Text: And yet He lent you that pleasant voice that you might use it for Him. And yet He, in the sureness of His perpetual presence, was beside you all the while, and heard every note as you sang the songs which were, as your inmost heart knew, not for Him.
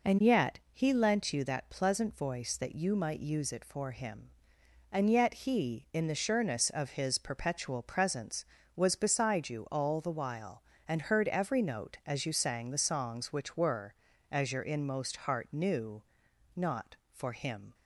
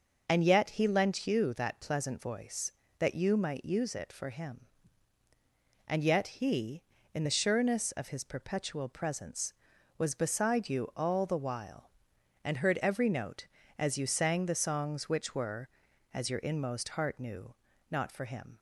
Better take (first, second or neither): neither